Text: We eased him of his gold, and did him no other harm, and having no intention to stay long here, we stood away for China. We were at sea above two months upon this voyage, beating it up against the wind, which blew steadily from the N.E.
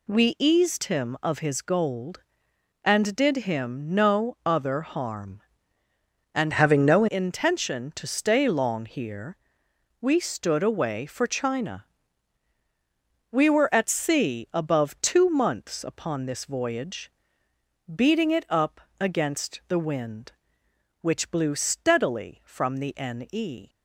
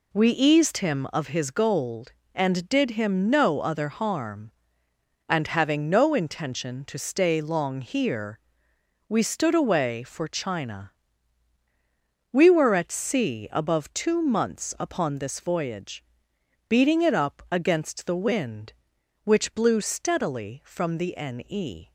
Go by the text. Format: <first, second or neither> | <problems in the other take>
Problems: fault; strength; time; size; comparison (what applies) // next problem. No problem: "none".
second | changes voice from "having" to "no"; from 6.5 to 7.0 s; 0.5 s long // pauses between "up" and "against"; slight; at 18.8 s; 0.18 s long